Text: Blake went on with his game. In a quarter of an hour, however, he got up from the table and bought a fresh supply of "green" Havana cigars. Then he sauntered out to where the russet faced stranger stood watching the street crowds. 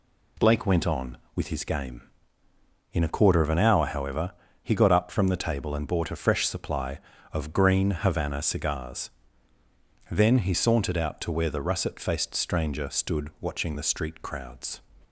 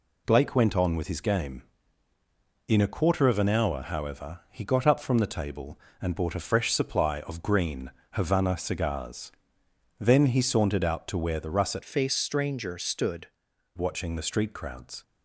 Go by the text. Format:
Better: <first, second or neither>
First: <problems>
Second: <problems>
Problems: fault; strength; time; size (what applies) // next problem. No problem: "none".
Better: first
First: none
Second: pauses between "green" and "Havana"; slight; at 7.9 s; 0.22 s long // changes voice from "faced" to "stood"; from 11.8 to 13.2 s; 1.4 s long